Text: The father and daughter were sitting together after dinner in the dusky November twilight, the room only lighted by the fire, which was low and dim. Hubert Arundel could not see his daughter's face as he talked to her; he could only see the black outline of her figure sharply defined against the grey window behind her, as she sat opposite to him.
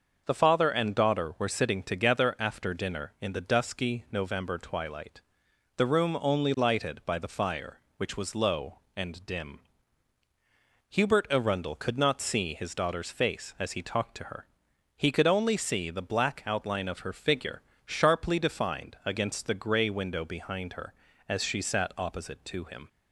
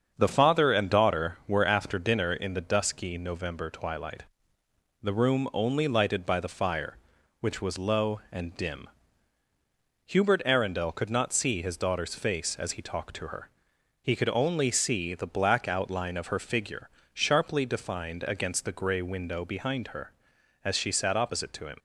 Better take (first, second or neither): first